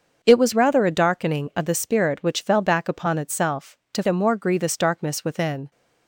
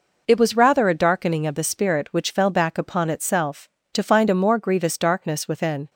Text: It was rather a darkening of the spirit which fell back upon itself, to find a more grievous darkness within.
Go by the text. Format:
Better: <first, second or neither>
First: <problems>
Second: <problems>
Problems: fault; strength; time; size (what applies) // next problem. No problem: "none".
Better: second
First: starts louder than the rest; until 1.2 s; 6.5 dB // skips "find"; at 4.0 s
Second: none